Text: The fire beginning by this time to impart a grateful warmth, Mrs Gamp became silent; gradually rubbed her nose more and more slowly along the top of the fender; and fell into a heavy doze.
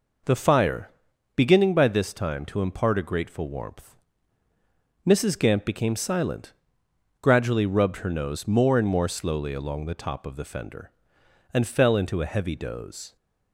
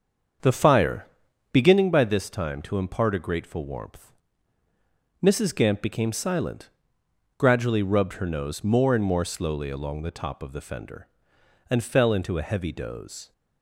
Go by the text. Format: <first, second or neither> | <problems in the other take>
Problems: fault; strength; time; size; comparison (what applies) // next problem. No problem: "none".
first | starts louder than the rest; until 1.9 s; 7 dB // pauses between "fire" and "beginning"; noticeable; at 1.0 s; 0.46 s long; noticeable in the first